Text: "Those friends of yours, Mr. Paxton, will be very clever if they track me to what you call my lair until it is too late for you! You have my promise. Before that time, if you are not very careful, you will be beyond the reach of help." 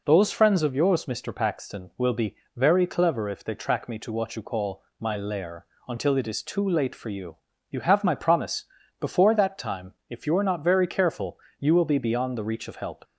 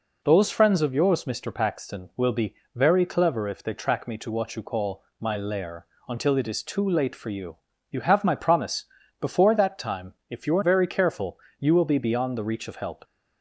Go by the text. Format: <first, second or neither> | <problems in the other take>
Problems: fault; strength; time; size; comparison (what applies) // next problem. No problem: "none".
first | pauses between "be" and "very"; slight; at 2.5 s; 0.20 s long; slight in the first // pauses between "call" and "my"; slight; at 5.0 s; 0.16 s long; slight in the first // pauses between "lair" and "until"; slight; at 5.8 s; 0.24 s long; slight in the first // skips "not"; at 10.6 s